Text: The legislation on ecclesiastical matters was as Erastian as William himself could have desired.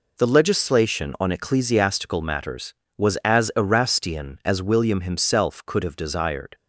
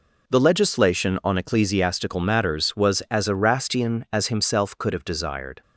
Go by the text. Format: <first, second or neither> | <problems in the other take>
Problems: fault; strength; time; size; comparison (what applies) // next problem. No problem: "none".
first | skips "William"; at 4.2 s